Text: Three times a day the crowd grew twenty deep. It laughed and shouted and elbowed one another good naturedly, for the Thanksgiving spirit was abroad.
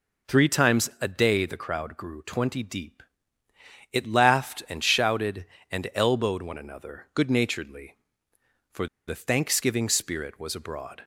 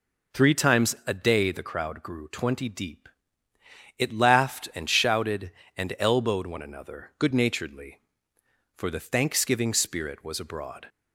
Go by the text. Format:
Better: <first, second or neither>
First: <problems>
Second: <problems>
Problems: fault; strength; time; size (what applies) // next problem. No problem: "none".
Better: second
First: pauses between "for" and "the"; slight; at 8.8 s; 0.20 s long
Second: none